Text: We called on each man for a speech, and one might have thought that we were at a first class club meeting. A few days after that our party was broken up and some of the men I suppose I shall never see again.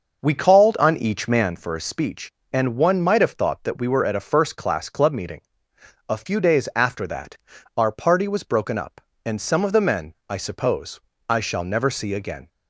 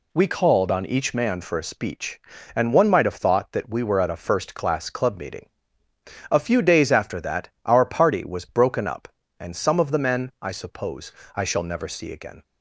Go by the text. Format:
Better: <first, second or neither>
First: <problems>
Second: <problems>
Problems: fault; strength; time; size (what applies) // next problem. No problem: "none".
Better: second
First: starts louder than the rest; noticeable; until 1.7 s; 6 dB // pauses between "that" and "our"; at 7.3 s; 0.40 s long // pauses between "men" and "I"; slight; at 10.1 s; 0.16 s long // pauses between "suppose" and "I"; slight; at 11.0 s; 0.26 s long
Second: pauses between "suppose" and "I"; slight; at 11.1 s; 0.24 s long